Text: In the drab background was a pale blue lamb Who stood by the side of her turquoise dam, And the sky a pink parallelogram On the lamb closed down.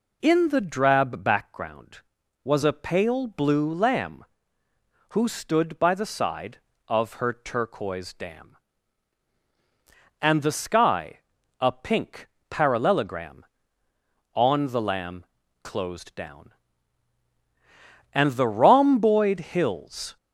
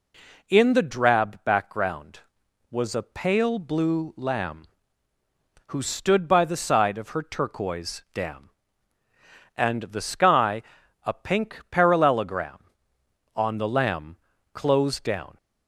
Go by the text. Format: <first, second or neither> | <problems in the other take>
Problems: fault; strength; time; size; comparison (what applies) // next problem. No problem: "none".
second | pauses between "sky" and "a"; at 11.2 s; 0.38 s long; also in the second // pauses between "pink" and "parallelogram"; slight; at 12.2 s; 0.22 s long // pauses between "lamb" and "closed"; at 15.2 s; 0.38 s long; also in the second // goes on to say "And the rhomboid hills"; strong; from 18.1 s on; 2.0 s long